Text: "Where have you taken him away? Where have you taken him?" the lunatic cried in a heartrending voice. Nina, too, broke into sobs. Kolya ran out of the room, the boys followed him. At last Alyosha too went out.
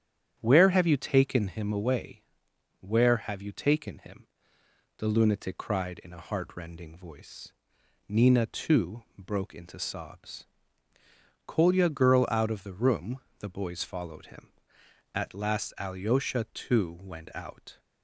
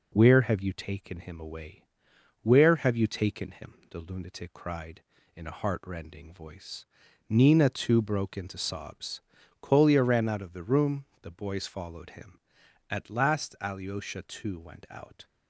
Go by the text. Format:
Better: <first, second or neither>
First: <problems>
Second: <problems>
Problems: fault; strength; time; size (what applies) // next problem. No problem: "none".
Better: second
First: starts louder than the rest; strong; until 1.4 s; 9.5 dB // says "girl" for "ran"; at 11.8 s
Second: none